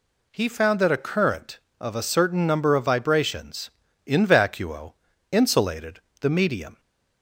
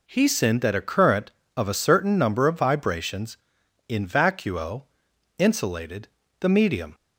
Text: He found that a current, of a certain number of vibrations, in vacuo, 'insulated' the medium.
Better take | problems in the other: first | says "sinned" for "found"; at 0.2 s // pauses between "insulated" and "the"; slight; at 6.0 s; 0.32 s long; slight in the first

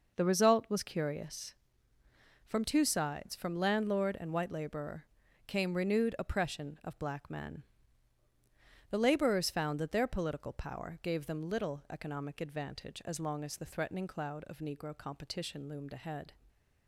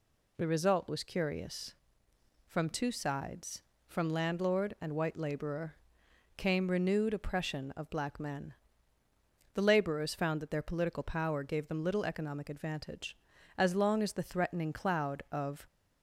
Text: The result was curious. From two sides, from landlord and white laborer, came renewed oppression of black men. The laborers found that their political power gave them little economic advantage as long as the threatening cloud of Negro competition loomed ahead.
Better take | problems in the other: first | stops before "Negro competition loomed ahead"; at 15.6 s

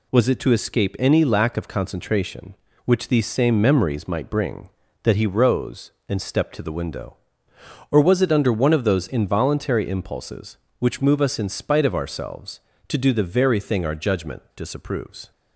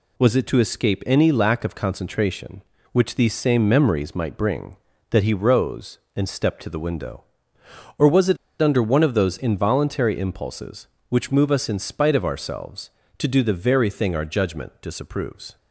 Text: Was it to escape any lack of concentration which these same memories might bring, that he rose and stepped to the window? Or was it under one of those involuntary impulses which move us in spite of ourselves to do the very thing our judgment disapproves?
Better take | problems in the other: first | pauses between "it" and "under"; slight; at 8.3 s; 0.24 s long

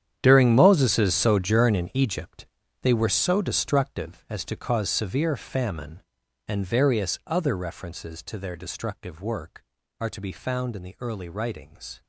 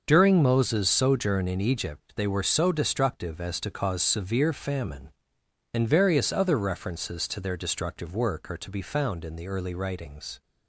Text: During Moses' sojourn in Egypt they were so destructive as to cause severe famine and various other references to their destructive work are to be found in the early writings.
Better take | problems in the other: second | gets quieter; strong; throughout; 15.5 dB // starts louder than the rest; strong; until 1.2 s; 9.5 dB; also in the second // pauses between "Egypt" and "they"; slight; at 2.4 s; 0.36 s long

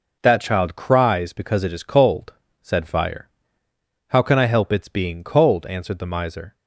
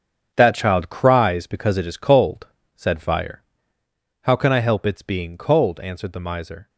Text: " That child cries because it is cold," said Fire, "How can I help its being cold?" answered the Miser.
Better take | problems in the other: first | gets quieter; strong; throughout; 9.5 dB

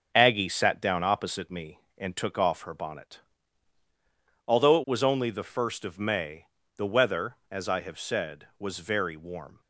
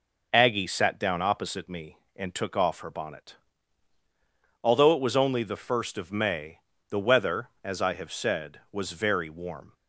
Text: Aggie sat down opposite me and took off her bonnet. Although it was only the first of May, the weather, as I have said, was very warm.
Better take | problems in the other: second | gets quieter; noticeable; throughout; 5.5 dB

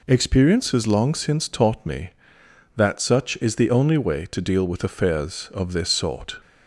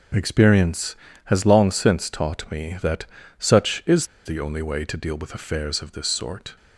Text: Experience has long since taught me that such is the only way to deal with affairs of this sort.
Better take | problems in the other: first | pauses between "that" and "such"; slight; at 3.0 s; 0.34 s long // pauses between "is" and "the"; slight; at 4.0 s; 0.20 s long

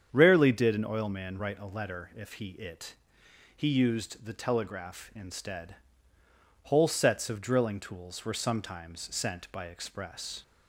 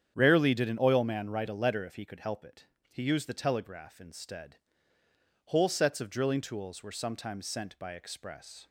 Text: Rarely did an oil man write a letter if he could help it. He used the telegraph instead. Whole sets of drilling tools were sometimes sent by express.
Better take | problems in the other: second | starts louder than the rest; strong; until 1.1 s; 8 dB; strong in the second // skips "could help"; at 2.5 s

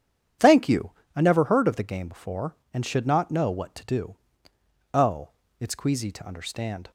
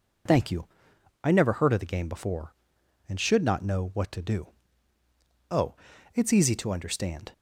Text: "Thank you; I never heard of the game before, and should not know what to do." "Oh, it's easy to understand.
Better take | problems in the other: second | starts louder than the rest; strong; until 1.6 s; 9 dB // says "queasy" for "easy"; at 5.7 s

